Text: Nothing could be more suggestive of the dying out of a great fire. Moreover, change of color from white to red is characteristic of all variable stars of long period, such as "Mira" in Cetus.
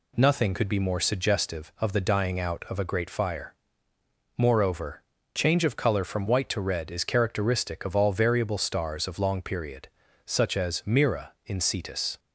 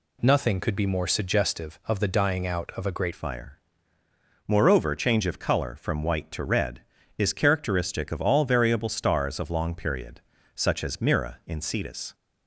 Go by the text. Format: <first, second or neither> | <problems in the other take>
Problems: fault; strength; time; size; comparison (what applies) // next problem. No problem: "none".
first | changes voice at "fire"; from 3.1 s on; 9.0 s long